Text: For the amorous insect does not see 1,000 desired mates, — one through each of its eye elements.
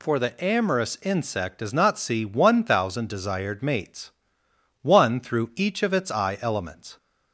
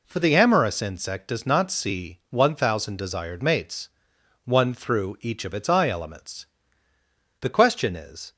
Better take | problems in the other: first | goes on to say "The question is"; noticeable; from 7.3 s on; 0.94 s long

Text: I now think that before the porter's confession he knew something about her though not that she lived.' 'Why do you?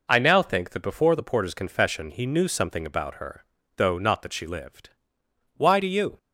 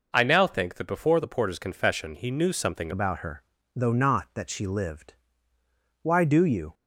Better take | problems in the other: first | changes voice at "about"; from 2.9 s on; 3.8 s long // pauses between "her" and "though"; slight; at 3.4 s; 0.32 s long; slight in the first

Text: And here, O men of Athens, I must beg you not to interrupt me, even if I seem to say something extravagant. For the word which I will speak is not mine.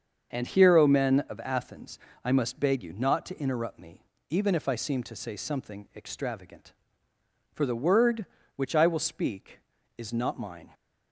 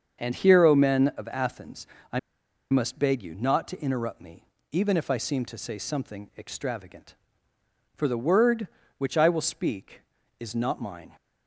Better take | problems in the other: first | starts louder than the rest; until 1.2 s; 6.5 dB; also in the first // pauses between "I" and "must"; noticeable; at 2.1 s; 0.51 s long

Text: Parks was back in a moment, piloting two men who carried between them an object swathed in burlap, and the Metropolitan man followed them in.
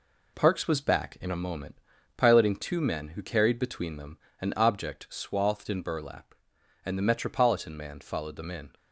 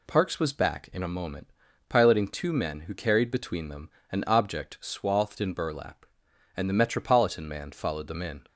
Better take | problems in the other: second | gets quieter; noticeable; throughout; 5 dB // pauses between "them" and "an"; slight; at 4.1 s; 0.24 s long; slight in the second

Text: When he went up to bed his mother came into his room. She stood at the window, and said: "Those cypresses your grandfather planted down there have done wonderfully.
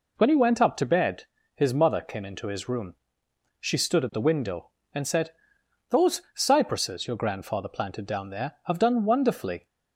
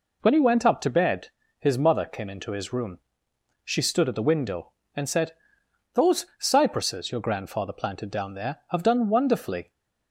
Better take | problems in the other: neither | pauses between "bed" and "his"; slight; the same in both

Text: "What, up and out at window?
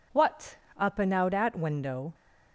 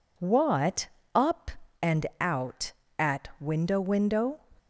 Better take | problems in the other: first | pauses between "and" and "out"; slight; at 2.0 s; 0.16 s long // says "window" twice; at 3.8 s

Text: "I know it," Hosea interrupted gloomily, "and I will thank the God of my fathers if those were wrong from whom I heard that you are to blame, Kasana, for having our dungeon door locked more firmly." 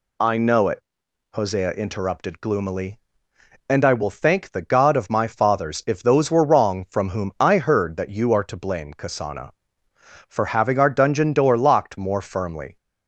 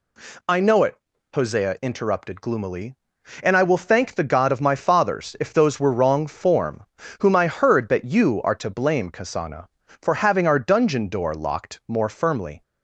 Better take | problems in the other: first | says "form" for "from"; at 6.2 s

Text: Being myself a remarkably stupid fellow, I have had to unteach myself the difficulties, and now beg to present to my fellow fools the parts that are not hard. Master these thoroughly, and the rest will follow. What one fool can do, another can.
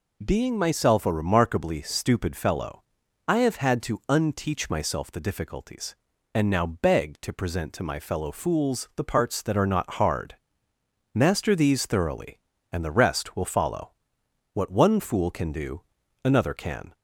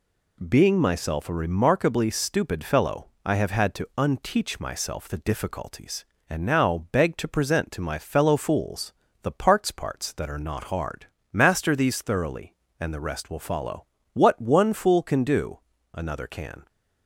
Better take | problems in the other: first | pauses between "fools" and "the"; slight; at 8.9 s; 0.30 s long // says "parts" twice; at 9.7 s

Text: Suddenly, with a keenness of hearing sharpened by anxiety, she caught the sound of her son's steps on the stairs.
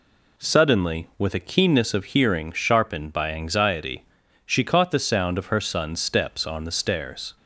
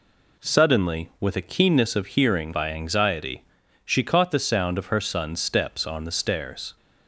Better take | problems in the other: first | skips "sharpened"; at 2.5 s

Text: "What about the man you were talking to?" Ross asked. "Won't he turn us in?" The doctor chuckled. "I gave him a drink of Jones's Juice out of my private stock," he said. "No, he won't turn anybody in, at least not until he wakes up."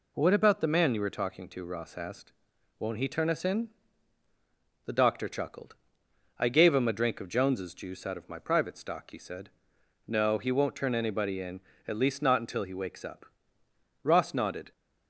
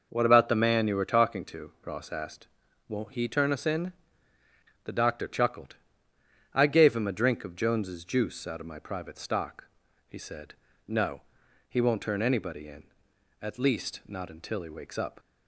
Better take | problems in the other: second | goes on to say "Ross nodded"; noticeable; from 14.0 s on; 0.68 s long

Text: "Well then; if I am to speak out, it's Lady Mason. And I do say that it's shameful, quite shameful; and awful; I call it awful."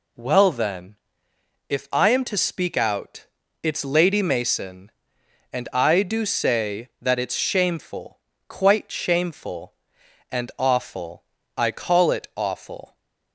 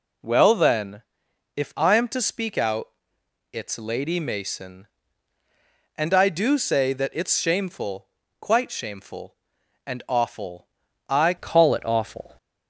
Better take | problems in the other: first | changes voice at "call"; from 11.3 s on; 1.0 s long

